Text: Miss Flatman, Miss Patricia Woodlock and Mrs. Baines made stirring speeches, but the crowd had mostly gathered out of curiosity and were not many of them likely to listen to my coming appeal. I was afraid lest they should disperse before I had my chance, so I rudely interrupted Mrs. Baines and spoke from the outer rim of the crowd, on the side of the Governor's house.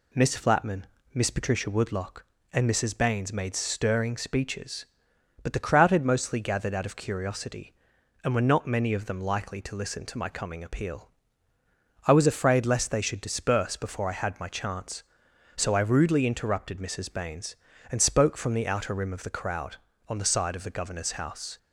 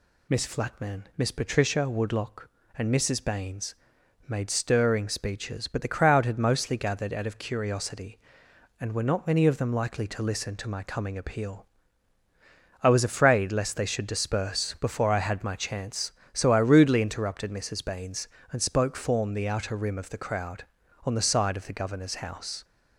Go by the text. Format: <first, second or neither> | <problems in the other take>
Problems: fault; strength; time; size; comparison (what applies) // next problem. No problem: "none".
first | pauses between "Baines" and "made"; noticeable; at 3.7 s; 0.52 s long // says "form" for "from"; at 18.9 s